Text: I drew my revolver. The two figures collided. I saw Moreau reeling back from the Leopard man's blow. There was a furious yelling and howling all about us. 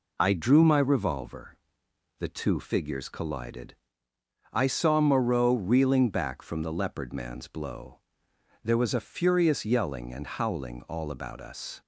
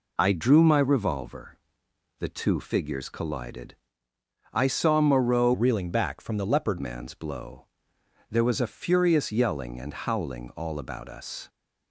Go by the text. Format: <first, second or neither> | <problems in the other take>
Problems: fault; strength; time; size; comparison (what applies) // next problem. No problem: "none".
first | changes voice from "reeling" to "Leopard"; from 5.5 to 6.7 s; 1.2 s long